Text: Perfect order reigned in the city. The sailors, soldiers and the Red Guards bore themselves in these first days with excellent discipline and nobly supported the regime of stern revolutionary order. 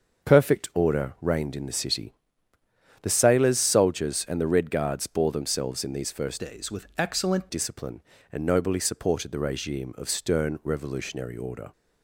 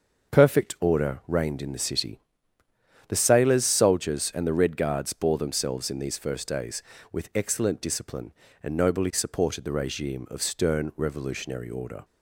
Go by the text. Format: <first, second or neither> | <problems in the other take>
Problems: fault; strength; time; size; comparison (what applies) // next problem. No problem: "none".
second | starts louder than the rest; until 1.3 s; 6.5 dB; also in the second // changes voice from "days" to "excellent"; from 6.3 to 7.4 s; 1.1 s long